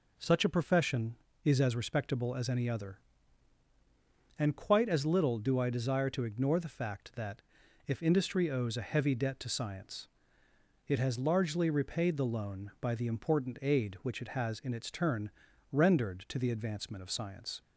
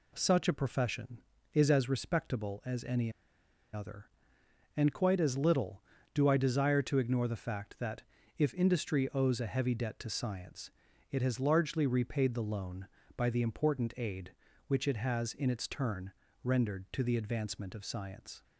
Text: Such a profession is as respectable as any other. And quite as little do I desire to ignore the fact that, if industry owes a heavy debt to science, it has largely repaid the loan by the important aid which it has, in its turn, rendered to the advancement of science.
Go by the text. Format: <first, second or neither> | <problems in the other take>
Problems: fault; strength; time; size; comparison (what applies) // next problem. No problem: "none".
first | pauses between "any" and "other"; noticeable; at 3.1 s; 0.63 s long